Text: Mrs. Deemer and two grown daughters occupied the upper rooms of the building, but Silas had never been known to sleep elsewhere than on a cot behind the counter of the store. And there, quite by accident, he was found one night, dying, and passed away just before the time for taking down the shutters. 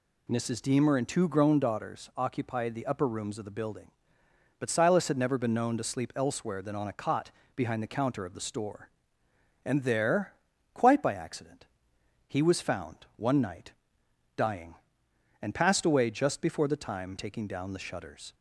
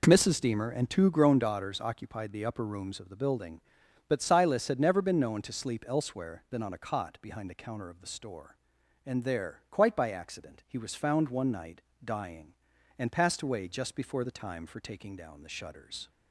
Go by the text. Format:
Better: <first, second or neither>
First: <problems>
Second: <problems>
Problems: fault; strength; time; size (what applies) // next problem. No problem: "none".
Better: second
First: pauses between "cot" and "behind"; slight; at 7.2 s; 0.26 s long // skips "for"; at 17.1 s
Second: none